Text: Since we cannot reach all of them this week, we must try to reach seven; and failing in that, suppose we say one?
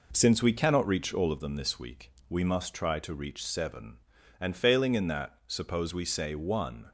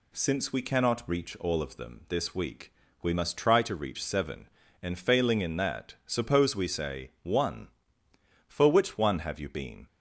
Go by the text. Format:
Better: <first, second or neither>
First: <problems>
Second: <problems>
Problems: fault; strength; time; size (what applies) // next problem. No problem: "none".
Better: first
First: none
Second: goes on to say "For which one have you been"; from 8.4 s on; 1.4 s long